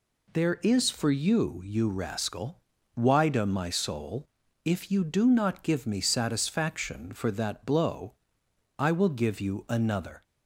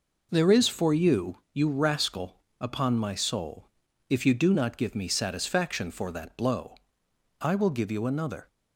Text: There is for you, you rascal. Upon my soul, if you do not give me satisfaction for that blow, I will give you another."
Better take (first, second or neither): second